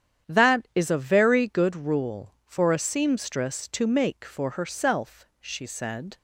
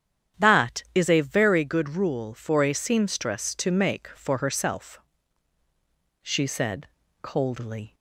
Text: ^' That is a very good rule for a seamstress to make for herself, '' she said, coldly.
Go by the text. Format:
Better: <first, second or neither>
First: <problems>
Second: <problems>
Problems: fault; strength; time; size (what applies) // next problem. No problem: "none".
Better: second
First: starts louder than the rest; strong; until 1.3 s; 9.5 dB // stops before "coldly"; at 6.1 s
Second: starts louder than the rest; strong; until 1.5 s; 10 dB